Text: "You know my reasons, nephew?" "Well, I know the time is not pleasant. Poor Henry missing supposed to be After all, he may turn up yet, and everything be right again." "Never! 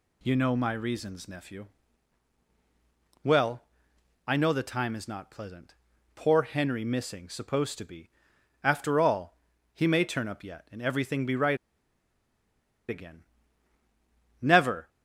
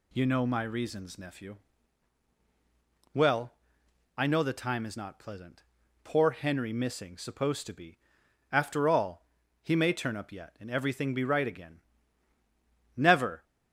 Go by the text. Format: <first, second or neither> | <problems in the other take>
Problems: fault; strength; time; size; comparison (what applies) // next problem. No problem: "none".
second | pauses between "be" and "After"; noticeable; at 8.1 s; 0.52 s long; noticeable in the second // pauses between "right" and "again"; strong; at 11.5 s; 1.3 s long